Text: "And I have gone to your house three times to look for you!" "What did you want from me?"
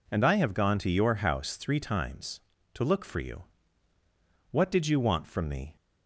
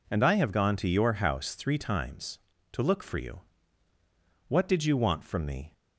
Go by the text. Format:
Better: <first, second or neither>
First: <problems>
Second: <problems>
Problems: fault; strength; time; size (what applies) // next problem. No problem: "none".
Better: neither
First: none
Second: none